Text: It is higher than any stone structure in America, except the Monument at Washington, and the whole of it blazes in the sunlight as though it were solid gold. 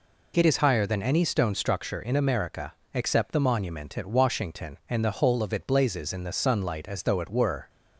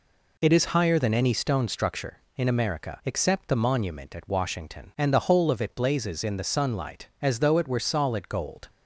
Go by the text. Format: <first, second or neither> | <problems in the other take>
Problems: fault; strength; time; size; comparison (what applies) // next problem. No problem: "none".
second | stops before "solid gold"; at 7.6 s